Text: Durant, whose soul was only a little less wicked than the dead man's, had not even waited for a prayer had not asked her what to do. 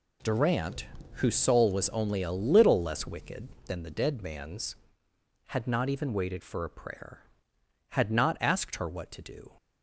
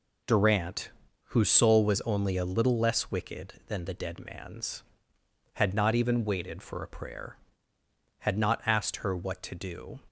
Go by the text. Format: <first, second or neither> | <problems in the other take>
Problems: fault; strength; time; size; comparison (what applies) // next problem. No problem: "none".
neither | none